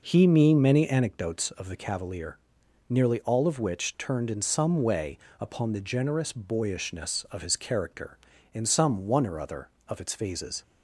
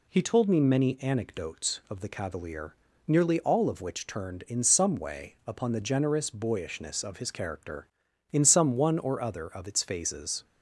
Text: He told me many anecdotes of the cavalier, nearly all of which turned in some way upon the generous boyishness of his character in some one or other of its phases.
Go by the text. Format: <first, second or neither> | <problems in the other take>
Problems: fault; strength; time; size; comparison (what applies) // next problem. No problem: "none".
second | skips "told"; at 0.2 s // pauses between "way" and "upon"; slight; at 5.1 s; 0.22 s long